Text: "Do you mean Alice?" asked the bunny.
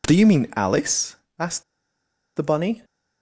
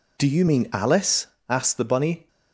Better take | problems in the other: second | pauses between "asked" and "the"; noticeable; at 1.6 s; 0.73 s long

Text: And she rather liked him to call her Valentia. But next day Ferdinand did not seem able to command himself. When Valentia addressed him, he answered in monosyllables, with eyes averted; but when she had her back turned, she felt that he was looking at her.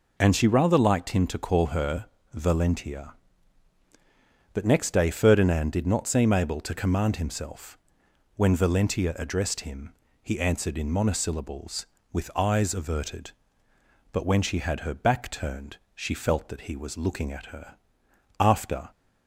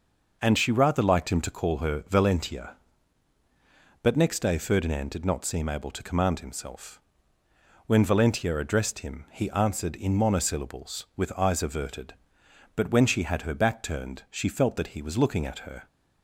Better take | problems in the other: second | pauses between "her" and "Valentia"; slight; at 2.0 s; 0.26 s long // goes on to say "After"; from 18.3 s on; 0.52 s long

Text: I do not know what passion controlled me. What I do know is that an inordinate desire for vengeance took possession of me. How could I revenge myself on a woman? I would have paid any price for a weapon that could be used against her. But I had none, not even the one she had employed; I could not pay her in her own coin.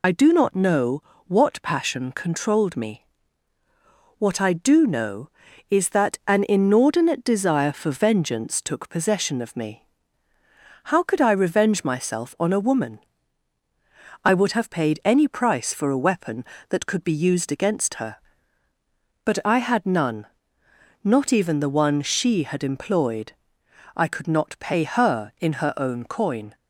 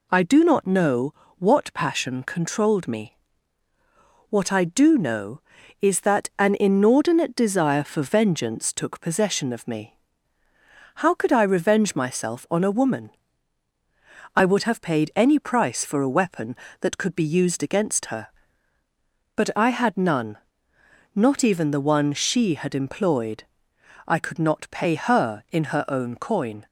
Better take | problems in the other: second | loses the start of "I"; at 0.0 s; 55 ms // pauses between "know" and "what"; slight; at 1.0 s; 0.24 s long; slight in the second

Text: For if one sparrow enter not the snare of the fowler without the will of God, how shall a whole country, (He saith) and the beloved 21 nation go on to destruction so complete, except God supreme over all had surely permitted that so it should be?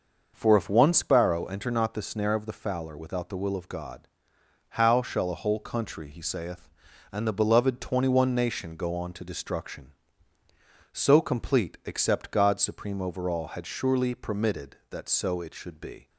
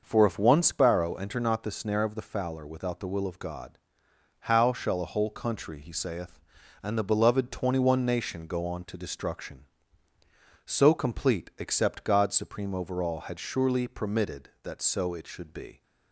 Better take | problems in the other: neither | starts louder than the rest; noticeable; the same in both

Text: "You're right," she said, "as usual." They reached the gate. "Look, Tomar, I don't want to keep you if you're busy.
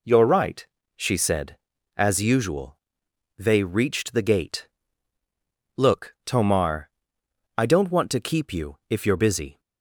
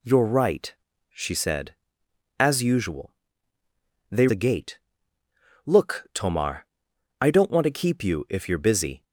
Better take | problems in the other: first | skips "reached"; at 4.2 s

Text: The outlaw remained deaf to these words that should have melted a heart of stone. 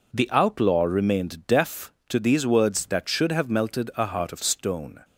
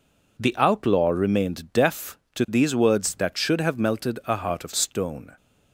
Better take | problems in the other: neither | none

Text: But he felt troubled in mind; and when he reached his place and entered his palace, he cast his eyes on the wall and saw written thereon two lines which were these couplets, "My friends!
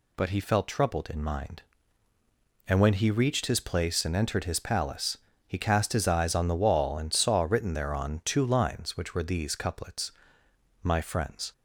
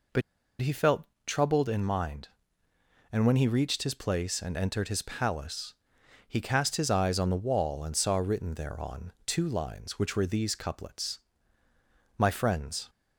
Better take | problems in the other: first | pauses between "But" and "he"; at 0.2 s; 0.39 s long // pauses between "felt" and "troubled"; slight; at 1.0 s; 0.20 s long

